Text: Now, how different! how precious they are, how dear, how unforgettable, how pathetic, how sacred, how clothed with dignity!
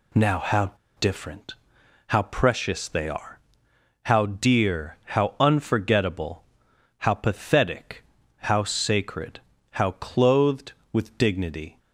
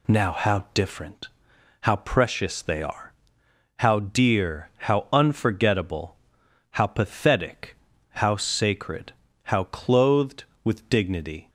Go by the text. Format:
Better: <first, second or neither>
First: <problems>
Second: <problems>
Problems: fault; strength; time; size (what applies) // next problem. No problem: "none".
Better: second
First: pauses between "how" and "different"; slight; at 0.7 s; 0.27 s long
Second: none